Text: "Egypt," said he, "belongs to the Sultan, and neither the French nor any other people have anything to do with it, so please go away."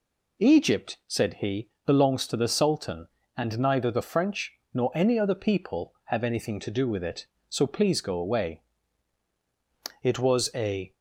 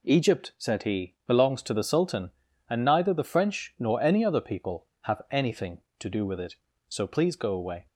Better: second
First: pauses between "French" and "nor"; slight; at 4.5 s; 0.18 s long // goes on to say "It was a"; noticeable; from 10.0 s on; 0.90 s long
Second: none

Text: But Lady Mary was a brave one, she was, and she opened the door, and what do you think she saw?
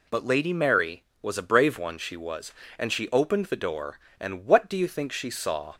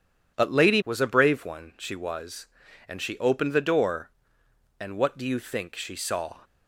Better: first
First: none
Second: skips "Mary"; at 0.8 s

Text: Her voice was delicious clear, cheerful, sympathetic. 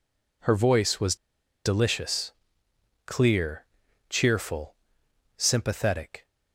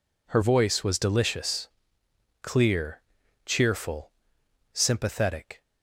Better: second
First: pauses between "was" and "delicious"; noticeable; at 1.1 s; 0.49 s long // pauses between "delicious" and "clear"; noticeable; at 2.3 s; 0.74 s long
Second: pauses between "delicious" and "clear"; noticeable; at 1.6 s; 0.74 s long

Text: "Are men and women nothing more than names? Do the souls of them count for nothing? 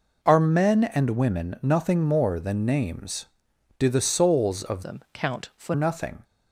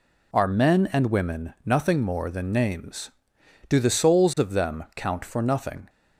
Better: second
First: changes voice from "them" to "for"; from 4.8 to 5.7 s; 0.9 s long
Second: none

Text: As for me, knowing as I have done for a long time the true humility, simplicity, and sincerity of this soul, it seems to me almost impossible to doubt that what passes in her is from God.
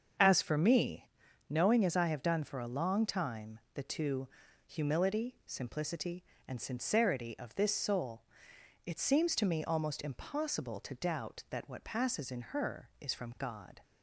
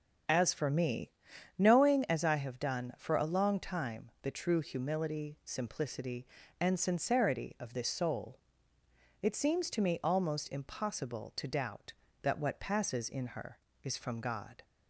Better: second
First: starts louder than the rest; until 1.6 s; 6.5 dB // pauses between "time" and "the"; slight; at 3.5 s; 0.16 s long // says "two" for "true"; at 3.8 s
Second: starts louder than the rest; until 1.7 s; 7 dB

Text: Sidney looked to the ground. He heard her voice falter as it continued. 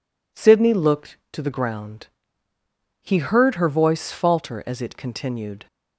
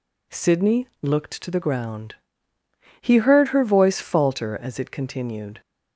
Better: neither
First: none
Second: none

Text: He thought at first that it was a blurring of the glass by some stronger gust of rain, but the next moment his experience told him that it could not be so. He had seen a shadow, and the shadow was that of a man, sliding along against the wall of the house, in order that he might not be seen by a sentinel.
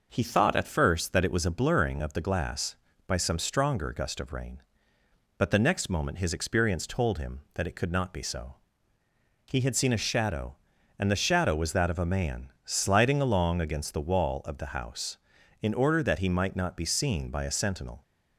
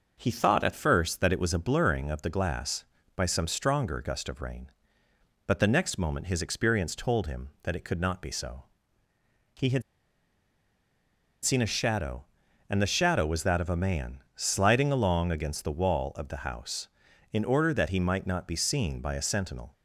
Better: first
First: none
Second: pauses between "had" and "seen"; strong; at 9.8 s; 1.6 s long

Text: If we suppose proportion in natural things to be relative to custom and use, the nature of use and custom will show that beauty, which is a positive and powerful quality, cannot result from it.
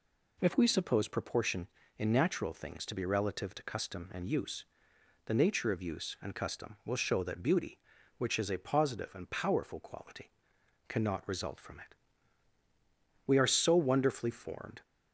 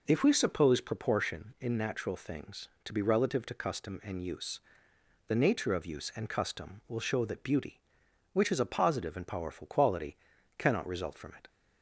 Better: second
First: goes on to say "We are so wonderfully formed"; from 13.2 s on; 1.5 s long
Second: none

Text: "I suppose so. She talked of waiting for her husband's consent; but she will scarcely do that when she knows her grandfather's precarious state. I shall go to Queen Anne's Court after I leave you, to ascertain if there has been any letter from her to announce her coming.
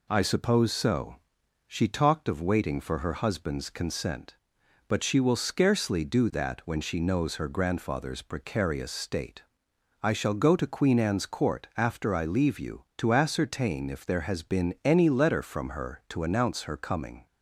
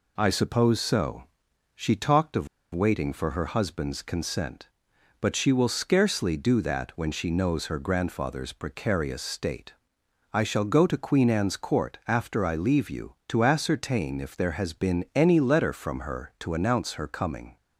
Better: first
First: none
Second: pauses between "of" and "waiting"; slight; at 2.4 s; 0.26 s long

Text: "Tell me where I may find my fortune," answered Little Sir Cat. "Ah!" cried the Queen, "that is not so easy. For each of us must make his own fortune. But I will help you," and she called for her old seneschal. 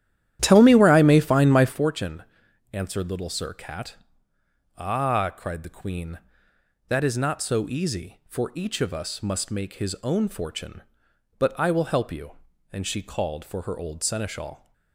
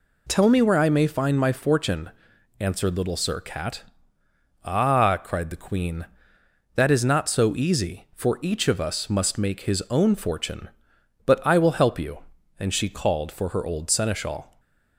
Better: second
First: starts louder than the rest; strong; until 1.9 s; 11.5 dB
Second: none

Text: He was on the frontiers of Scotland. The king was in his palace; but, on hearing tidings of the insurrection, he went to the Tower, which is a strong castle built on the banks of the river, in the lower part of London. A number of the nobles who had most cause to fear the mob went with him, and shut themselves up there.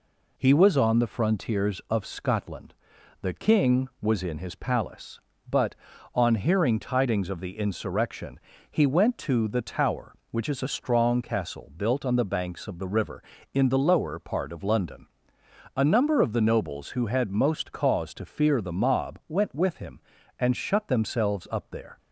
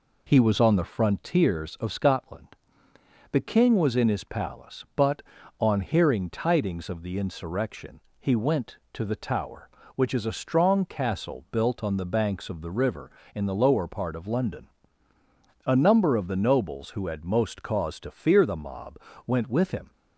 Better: first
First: none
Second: pauses between "mob" and "went"; slight; at 18.9 s; 0.28 s long // stops before "and shut themselves up there"; at 19.9 s

